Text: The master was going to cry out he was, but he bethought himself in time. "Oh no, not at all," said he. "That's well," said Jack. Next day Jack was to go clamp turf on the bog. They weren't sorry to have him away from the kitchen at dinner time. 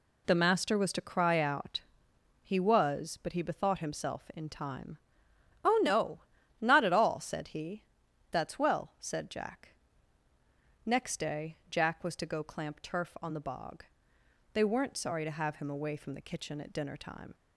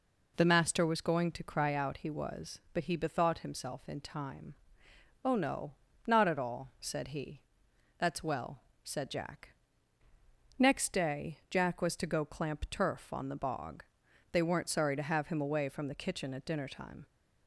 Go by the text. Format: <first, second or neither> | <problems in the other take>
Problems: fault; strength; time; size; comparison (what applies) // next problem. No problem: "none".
second | skips "going"; at 0.9 s // pauses between "out" and "he"; noticeable; at 1.8 s; 0.60 s long